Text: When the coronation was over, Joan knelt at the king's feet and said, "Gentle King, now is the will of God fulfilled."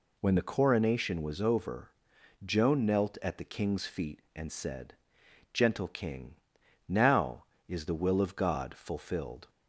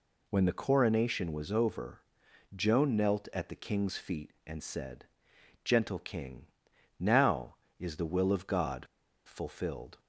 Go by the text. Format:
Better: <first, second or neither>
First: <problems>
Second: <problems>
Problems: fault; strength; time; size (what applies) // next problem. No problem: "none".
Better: first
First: none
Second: pauses between "God" and "fulfilled"; at 8.8 s; 0.39 s long